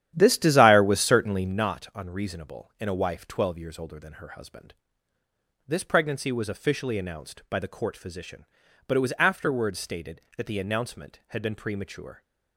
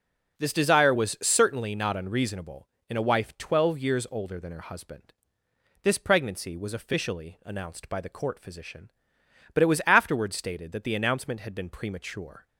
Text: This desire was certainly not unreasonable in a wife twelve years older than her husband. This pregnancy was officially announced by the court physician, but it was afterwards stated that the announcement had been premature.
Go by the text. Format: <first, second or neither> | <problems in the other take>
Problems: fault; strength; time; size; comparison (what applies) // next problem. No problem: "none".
second | starts louder than the rest; strong; until 1.7 s; 11 dB